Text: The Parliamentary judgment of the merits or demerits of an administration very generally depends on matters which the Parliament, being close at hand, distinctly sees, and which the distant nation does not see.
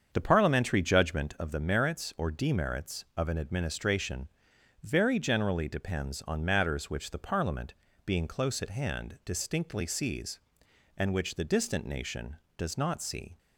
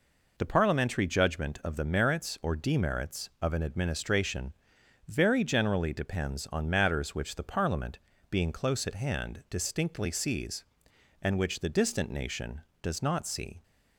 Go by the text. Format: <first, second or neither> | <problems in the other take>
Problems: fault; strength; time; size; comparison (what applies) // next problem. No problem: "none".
second | starts louder than the rest; strong; until 1.3 s; 7 dB // pauses between "administration" and "very"; noticeable; at 4.2 s; 0.56 s long; noticeable in the second